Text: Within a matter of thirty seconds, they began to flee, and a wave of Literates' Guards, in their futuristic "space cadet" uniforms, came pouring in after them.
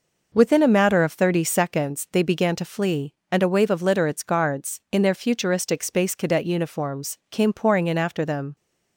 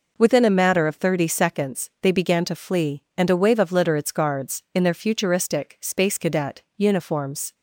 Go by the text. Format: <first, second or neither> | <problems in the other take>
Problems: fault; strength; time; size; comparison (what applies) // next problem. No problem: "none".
first | stops before "came pouring in after them"; at 7.5 s